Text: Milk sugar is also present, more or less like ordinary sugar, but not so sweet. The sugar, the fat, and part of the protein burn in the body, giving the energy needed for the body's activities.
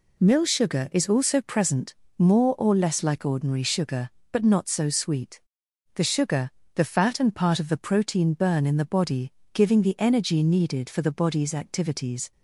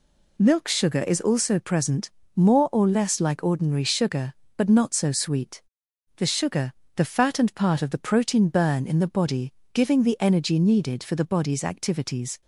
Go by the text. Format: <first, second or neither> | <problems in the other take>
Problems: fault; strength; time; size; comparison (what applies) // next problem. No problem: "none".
second | says "Mill" for "Milk"; at 0.1 s